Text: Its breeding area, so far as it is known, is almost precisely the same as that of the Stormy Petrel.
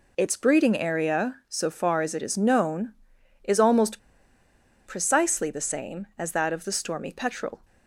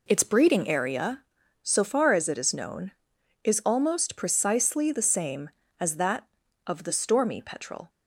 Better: second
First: pauses between "almost" and "precisely"; noticeable; at 3.9 s; 0.87 s long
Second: none

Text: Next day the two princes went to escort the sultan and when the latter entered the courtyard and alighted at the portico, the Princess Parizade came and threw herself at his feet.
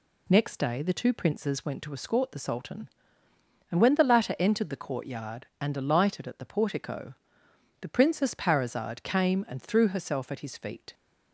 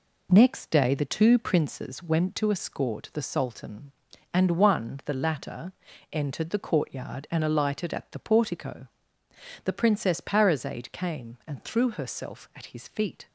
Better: first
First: none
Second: says "one" for "when"; at 4.5 s // pauses between "latter" and "entered"; at 5.7 s; 0.40 s long

